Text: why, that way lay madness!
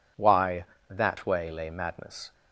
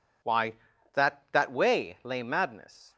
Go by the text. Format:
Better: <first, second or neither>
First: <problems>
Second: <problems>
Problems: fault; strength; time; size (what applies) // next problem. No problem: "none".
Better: first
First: none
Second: says "that" twice; at 1.3 s